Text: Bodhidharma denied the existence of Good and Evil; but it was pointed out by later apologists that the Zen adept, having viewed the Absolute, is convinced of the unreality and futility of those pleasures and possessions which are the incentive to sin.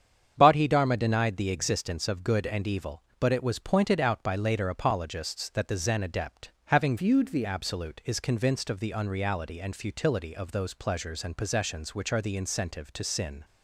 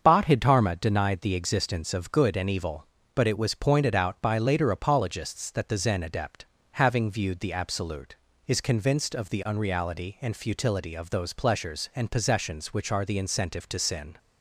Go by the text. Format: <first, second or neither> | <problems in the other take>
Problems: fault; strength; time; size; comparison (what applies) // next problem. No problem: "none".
second | starts louder than the rest; strong; until 1.3 s; 8 dB; also in the second // changes voice from "viewed" to "the"; from 6.9 to 7.4 s; 0.5 s long